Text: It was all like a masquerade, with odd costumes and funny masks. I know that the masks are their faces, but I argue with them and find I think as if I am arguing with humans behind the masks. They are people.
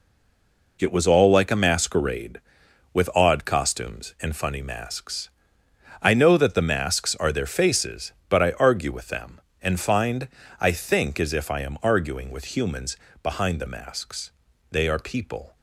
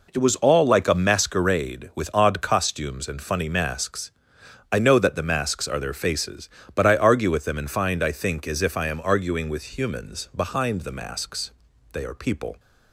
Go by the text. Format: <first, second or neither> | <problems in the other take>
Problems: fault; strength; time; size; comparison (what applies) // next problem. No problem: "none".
second | stays silent before the first word; slight; until 0.7 s; 0.7 s long // pauses between "find" and "I"; slight; at 10.2 s; 0.32 s long // pauses between "humans" and "behind"; slight; at 12.9 s; 0.28 s long